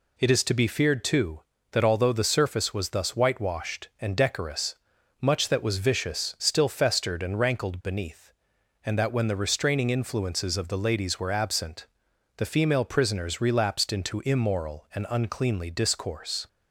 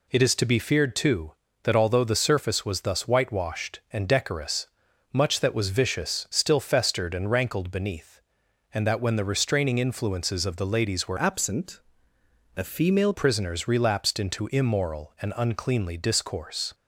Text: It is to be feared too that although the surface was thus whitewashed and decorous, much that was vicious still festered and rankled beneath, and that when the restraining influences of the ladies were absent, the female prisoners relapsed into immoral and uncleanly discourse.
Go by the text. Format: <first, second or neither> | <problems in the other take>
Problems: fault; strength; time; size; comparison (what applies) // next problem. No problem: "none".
first | changes voice from "absent" to "female"; from 11.1 to 13.1 s; 2.0 s long